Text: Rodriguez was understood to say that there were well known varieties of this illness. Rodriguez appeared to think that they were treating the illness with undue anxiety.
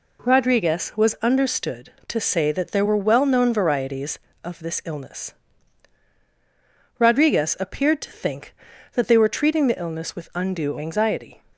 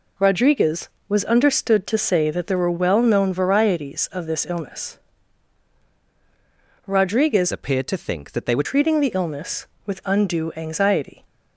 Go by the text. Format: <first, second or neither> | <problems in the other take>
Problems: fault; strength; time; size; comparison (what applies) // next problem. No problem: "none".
first | changes voice from "appeared" to "were"; from 7.5 to 8.6 s; 1.1 s long